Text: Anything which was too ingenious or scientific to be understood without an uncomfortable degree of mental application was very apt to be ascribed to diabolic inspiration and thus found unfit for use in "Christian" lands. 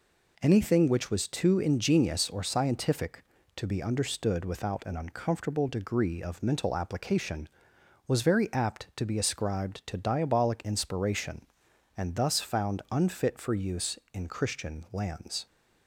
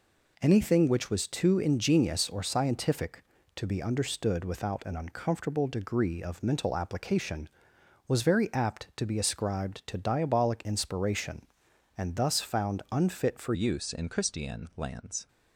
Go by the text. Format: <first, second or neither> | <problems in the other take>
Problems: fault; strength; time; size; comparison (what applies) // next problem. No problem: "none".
first | changes voice at "use"; from 13.5 s on; 1.7 s long